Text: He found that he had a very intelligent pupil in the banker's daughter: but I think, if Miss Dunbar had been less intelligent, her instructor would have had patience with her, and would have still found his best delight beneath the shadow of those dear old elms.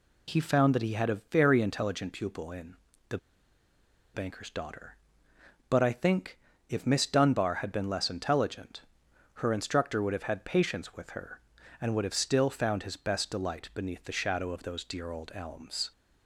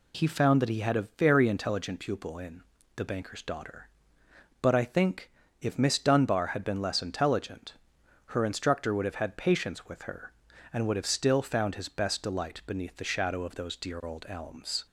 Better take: second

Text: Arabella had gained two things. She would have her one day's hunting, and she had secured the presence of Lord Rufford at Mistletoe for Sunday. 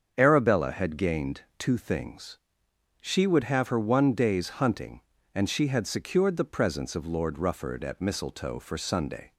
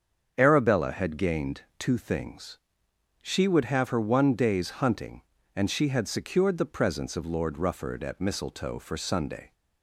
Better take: neither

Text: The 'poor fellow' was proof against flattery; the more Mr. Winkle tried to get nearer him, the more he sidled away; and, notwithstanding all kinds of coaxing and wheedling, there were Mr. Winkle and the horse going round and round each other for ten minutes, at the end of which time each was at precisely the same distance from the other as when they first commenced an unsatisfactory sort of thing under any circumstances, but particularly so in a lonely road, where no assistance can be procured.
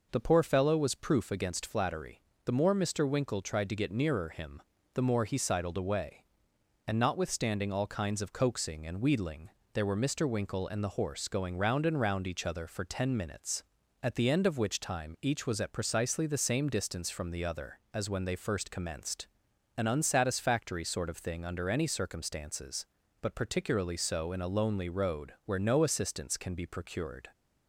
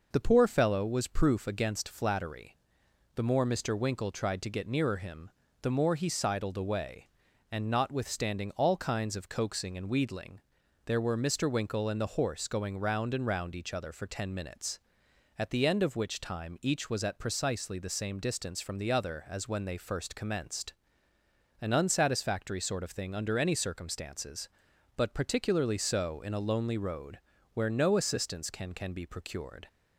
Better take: first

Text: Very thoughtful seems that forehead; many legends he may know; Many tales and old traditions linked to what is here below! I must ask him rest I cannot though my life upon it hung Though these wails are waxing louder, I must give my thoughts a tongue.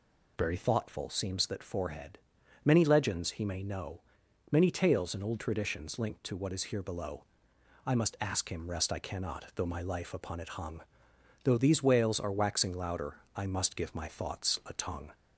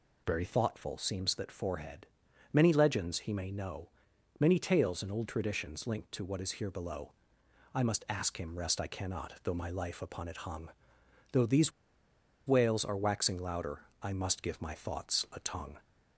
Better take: first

